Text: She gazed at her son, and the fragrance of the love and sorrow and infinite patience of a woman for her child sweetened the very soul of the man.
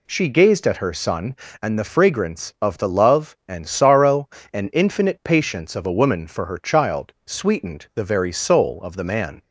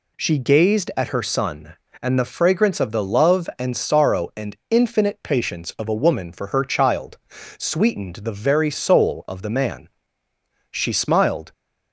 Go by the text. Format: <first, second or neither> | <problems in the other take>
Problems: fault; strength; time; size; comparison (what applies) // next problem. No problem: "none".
first | pauses between "child" and "sweetened"; at 7.1 s; 0.40 s long // goes on to say "She smiled"; noticeable; from 10.6 s on; 0.82 s long